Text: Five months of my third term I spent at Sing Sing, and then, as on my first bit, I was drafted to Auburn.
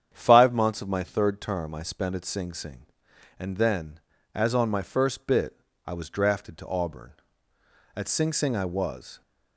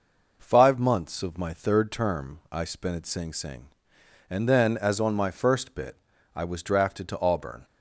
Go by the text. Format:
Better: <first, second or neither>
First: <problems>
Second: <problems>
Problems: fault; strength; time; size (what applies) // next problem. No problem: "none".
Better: second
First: starts louder than the rest; strong; until 1.1 s; 8.5 dB // goes on to say "At Sing Sing I was"; noticeable; from 7.9 s on; 1.2 s long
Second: none